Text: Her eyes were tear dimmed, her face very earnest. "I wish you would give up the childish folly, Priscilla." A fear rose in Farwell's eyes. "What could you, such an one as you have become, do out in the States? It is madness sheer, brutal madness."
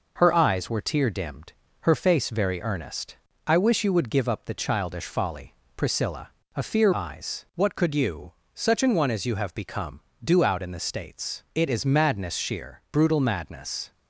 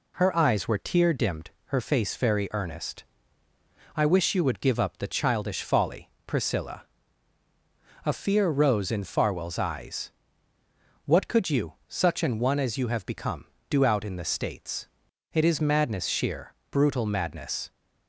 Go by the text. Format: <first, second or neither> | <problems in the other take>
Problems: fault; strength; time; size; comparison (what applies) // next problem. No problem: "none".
second | skips "rose in Farwell's"; at 6.9 s